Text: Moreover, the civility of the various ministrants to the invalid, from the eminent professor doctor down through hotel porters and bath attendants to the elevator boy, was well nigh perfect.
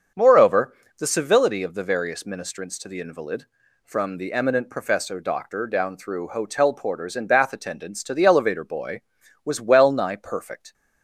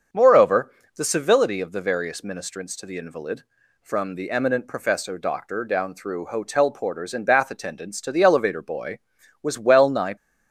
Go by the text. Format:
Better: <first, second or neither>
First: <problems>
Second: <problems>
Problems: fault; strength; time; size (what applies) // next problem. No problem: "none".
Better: first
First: starts louder than the rest; until 1.3 s; 6.5 dB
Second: starts louder than the rest; until 1.3 s; 6.5 dB // stops before "perfect"; at 10.1 s